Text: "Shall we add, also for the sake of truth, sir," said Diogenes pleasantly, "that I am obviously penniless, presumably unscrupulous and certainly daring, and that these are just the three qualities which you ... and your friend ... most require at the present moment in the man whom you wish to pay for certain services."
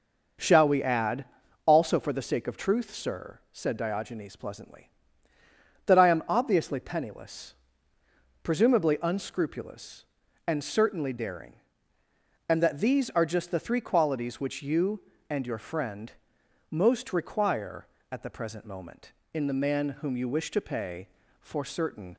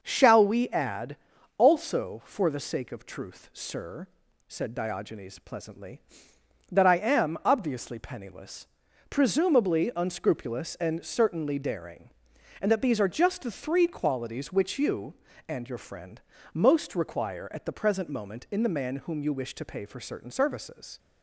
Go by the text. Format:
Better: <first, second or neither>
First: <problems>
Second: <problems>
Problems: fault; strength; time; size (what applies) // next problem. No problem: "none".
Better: second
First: starts louder than the rest; noticeable; until 1.8 s; 6 dB // stops before "services"; at 22.1 s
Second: starts louder than the rest; noticeable; until 1.0 s; 6 dB